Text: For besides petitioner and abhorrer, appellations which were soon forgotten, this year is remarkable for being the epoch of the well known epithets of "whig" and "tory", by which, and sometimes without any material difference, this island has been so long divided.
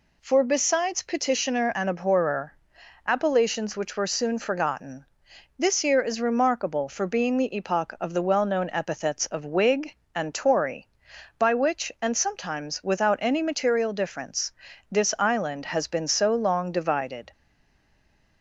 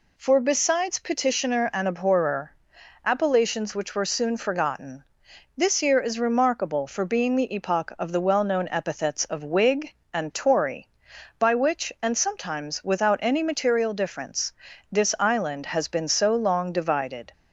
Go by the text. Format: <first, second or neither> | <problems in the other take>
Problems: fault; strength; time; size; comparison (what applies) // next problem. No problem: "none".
second | stays silent after the last word; from 17.3 s on; 1.1 s long